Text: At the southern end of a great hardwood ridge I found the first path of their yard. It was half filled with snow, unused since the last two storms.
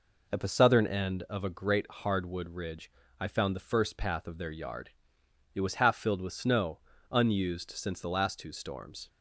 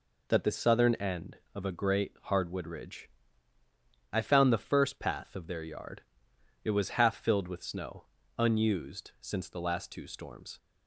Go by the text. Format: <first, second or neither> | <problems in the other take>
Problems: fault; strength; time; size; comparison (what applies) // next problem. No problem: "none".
first | says "That" for "At"; at 0.2 s // pauses between "ridge" and "I"; at 3.0 s; 1.0 s long; slight in the first